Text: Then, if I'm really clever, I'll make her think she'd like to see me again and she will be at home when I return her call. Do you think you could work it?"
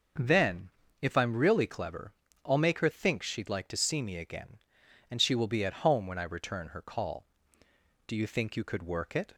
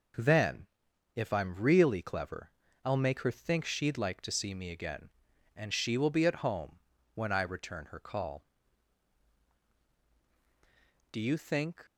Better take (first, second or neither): first